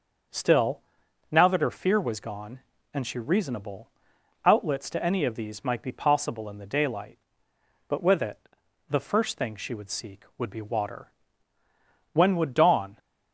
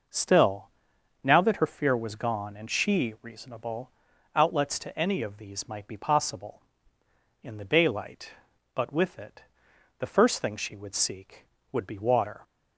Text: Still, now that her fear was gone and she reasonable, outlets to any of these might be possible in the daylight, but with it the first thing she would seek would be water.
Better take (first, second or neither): second